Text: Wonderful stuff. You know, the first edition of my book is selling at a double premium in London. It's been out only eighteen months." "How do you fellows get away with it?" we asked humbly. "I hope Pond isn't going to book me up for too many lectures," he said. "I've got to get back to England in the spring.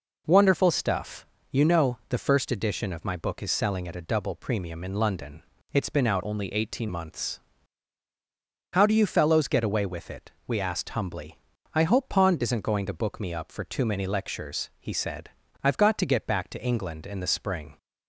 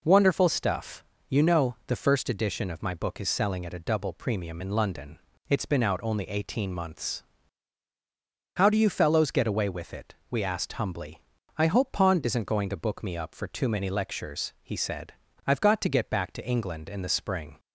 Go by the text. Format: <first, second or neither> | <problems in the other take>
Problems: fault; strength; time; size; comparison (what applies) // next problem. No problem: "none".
second | changes voice from "only" to "eighteen"; from 6.2 to 6.8 s; 0.6 s long